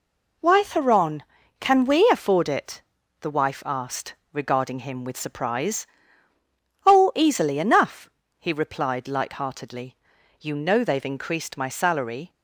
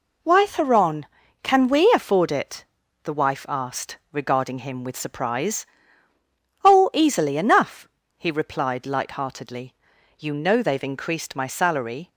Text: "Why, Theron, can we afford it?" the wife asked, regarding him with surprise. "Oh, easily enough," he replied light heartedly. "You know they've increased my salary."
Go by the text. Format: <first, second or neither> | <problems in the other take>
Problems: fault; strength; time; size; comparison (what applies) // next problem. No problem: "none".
neither | none